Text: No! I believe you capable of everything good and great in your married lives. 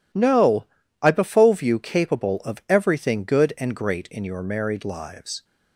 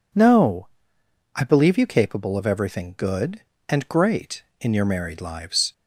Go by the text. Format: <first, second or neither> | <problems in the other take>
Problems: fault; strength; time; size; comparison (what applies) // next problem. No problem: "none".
second | says "befove" for "believe"; at 1.1 s